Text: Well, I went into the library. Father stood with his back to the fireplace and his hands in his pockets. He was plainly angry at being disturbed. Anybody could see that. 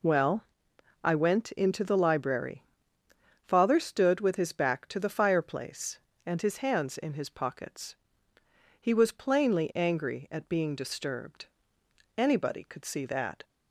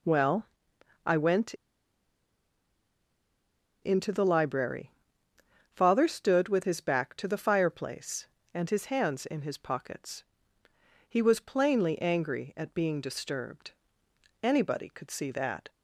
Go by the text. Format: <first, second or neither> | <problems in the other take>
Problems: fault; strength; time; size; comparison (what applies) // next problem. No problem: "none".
first | pauses between "went" and "into"; strong; at 1.5 s; 2.2 s long